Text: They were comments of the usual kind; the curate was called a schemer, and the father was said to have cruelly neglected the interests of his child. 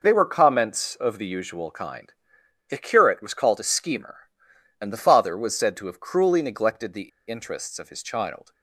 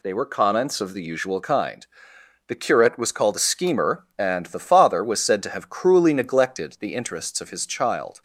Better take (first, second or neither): second